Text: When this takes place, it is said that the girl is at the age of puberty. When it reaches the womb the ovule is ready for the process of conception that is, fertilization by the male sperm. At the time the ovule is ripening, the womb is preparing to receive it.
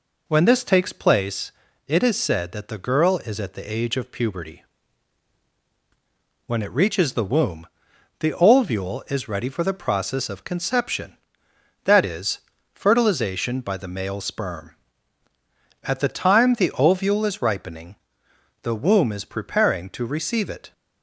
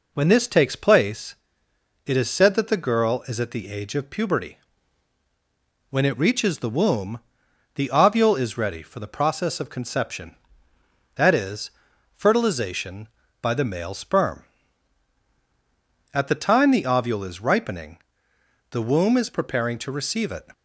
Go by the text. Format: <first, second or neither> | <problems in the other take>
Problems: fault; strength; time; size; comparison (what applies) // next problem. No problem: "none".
neither | pauses between "womb" and "the"; noticeable; the same in both